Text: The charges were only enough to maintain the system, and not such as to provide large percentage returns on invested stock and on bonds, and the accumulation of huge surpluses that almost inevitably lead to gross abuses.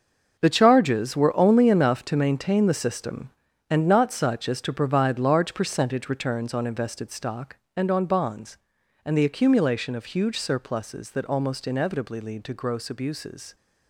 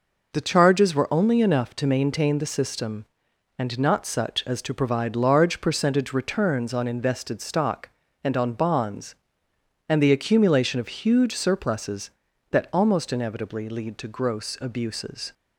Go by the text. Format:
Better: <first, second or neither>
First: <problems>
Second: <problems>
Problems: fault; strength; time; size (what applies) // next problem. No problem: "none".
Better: second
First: gets quieter; strong; throughout; 11 dB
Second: none